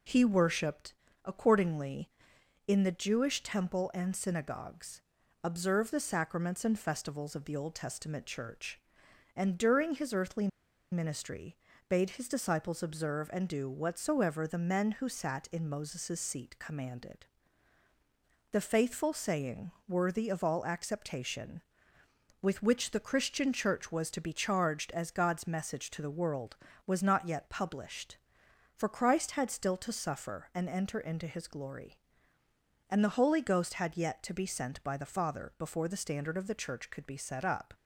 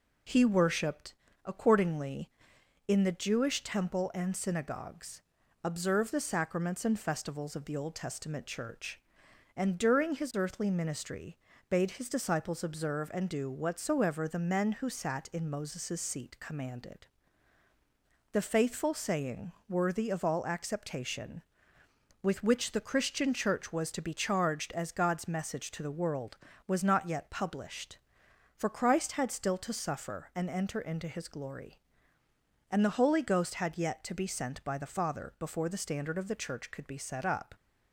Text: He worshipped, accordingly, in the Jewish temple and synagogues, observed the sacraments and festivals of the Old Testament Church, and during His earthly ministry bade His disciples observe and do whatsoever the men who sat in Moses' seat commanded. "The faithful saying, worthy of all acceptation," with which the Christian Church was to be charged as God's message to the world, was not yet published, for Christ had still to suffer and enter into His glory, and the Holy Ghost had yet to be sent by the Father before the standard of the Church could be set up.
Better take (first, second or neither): second